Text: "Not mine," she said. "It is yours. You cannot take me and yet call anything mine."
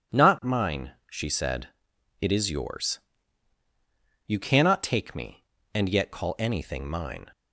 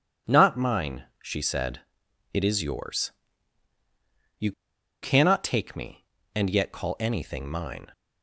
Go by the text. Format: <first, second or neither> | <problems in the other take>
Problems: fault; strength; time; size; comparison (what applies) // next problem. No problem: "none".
first | pauses between "You" and "cannot"; noticeable; at 4.5 s; 0.49 s long